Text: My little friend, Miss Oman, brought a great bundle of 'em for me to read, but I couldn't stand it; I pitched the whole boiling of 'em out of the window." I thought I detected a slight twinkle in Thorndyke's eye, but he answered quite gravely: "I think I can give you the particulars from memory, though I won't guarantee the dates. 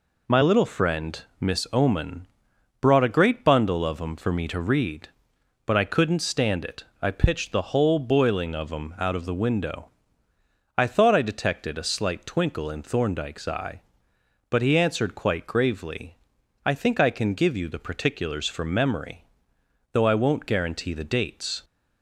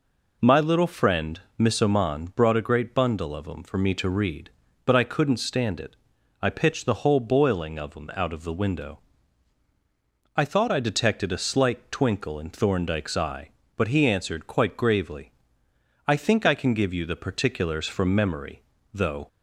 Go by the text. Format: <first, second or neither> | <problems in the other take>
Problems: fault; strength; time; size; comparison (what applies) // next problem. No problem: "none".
first | stops before "I won't guarantee the dates"; at 19.2 s